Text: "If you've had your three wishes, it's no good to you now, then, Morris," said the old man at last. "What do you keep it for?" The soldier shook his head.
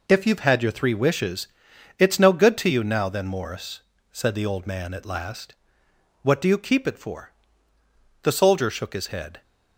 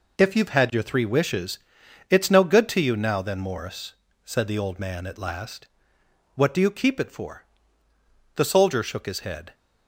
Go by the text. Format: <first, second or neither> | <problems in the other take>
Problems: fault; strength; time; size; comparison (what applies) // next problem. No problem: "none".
neither | none